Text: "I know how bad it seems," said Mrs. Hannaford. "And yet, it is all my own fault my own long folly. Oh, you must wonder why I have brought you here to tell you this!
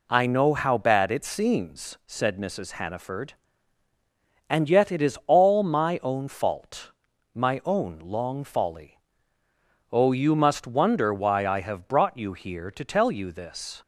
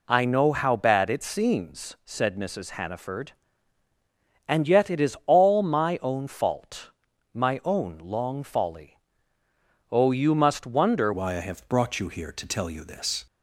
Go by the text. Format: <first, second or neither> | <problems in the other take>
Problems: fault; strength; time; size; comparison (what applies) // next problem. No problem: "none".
first | pauses between "fault" and "my"; at 6.9 s; 0.42 s long; also in the first // changes voice at "why"; from 11.1 s on; 2.1 s long